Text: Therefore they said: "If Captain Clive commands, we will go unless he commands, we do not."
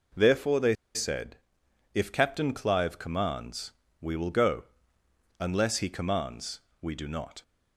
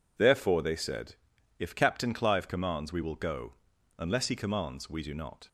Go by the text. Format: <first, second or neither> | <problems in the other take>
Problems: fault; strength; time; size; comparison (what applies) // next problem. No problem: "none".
second | pauses between "they" and "said"; slight; at 0.7 s; 0.19 s long // pauses between "go" and "unless"; noticeable; at 4.6 s; 0.74 s long; also in the second